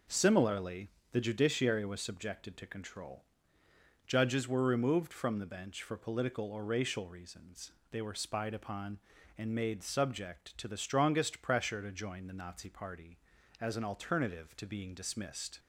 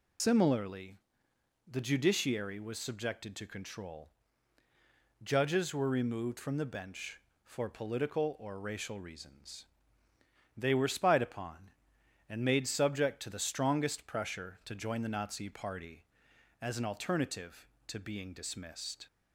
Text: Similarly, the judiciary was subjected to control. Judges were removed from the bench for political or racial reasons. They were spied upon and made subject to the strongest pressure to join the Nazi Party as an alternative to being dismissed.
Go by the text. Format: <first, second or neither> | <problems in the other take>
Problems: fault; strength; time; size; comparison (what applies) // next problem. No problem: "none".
first | loses the start of "Similarly"; at 0.1 s; 115 ms